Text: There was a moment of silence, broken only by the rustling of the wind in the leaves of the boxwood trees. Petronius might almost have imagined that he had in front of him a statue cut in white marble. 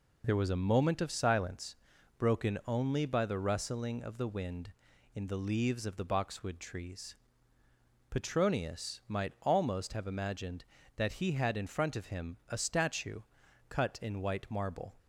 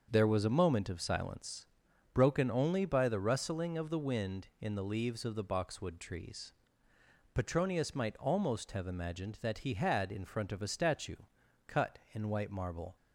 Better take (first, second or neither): first